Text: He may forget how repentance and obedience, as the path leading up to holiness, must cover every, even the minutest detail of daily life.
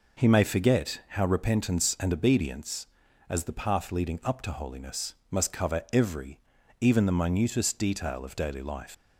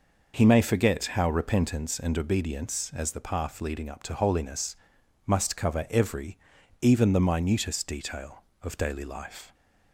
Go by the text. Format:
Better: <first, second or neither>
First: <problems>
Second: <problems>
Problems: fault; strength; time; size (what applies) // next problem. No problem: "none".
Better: second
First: leaves "life" unfinished; at 8.9 s; 150 ms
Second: none